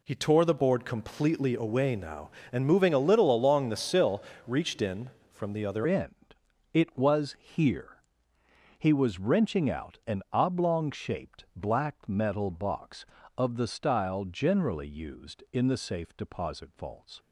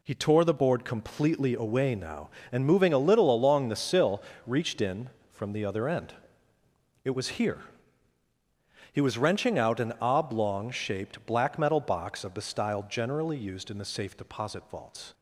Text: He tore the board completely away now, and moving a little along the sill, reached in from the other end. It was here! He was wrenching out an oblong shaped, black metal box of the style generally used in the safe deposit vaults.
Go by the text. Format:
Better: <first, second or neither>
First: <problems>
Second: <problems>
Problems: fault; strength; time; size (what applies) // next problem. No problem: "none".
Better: second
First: changes voice at "end"; from 5.8 s on; 11.3 s long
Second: none